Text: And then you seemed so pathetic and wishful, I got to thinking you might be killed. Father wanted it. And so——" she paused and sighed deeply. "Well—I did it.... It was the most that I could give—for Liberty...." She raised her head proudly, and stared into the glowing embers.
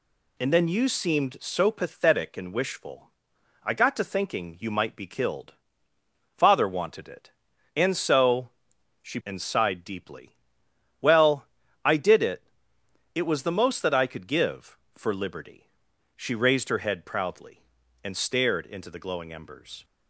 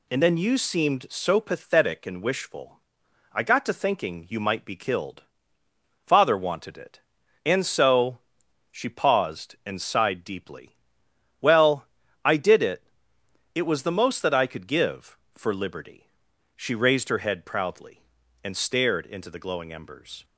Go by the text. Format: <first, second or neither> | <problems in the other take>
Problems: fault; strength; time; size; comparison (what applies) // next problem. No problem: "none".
second | skips "paused"; at 9.2 s